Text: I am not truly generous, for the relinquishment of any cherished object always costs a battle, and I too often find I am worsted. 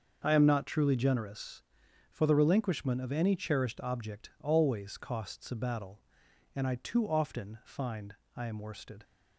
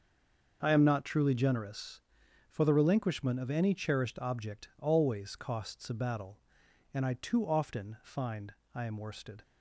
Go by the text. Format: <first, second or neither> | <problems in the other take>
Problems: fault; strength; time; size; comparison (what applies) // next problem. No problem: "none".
first | stays silent before the first word; slight; until 0.6 s; 0.6 s long // starts louder than the rest; until 1.6 s; 6 dB; also in the first // pauses between "find" and "I"; slight; at 8.5 s; 0.22 s long; slight in the first